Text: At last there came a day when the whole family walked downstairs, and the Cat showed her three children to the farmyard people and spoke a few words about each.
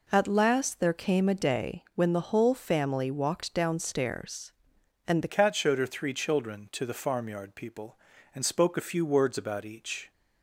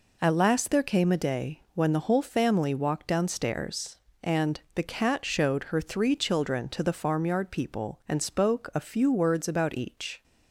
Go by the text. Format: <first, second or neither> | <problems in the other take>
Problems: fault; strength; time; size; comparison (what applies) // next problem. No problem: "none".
second | changes voice at "Cat"; from 5.2 s on; 4.9 s long